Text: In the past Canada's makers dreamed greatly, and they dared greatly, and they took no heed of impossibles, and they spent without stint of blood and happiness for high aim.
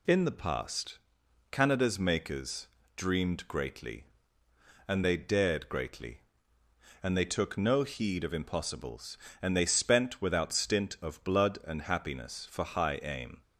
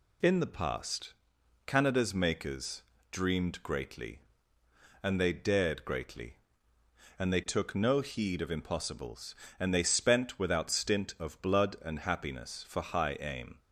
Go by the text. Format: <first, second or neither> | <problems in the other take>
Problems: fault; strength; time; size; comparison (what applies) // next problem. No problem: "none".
neither | pauses between "past" and "Canada's"; noticeable; the same in both // pauses between "makers" and "dreamed"; slight; the same in both